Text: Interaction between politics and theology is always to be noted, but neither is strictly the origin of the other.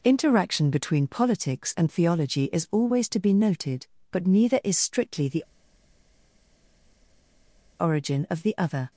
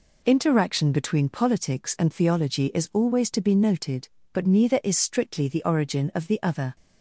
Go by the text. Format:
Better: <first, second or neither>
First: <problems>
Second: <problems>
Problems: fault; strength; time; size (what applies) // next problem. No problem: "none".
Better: second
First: pauses between "the" and "origin"; strong; at 5.4 s; 2.3 s long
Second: none